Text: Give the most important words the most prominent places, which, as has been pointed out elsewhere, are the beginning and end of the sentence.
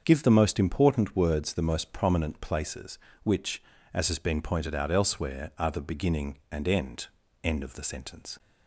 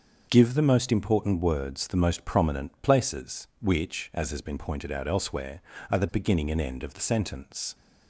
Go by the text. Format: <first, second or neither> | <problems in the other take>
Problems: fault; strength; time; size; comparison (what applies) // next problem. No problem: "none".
second | starts louder than the rest; until 1.0 s; 7 dB; also in the second // says "end" twice; at 7.4 s